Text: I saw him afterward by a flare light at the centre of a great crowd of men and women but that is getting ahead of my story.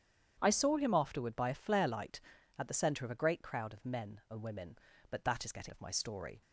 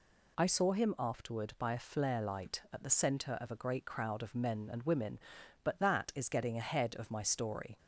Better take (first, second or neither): second